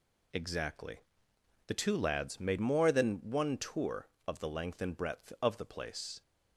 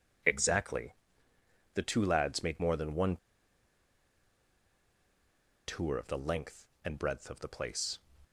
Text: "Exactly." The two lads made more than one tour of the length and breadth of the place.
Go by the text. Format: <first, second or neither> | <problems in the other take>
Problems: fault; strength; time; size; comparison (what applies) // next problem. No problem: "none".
first | pauses between "one" and "tour"; strong; at 3.1 s; 2.5 s long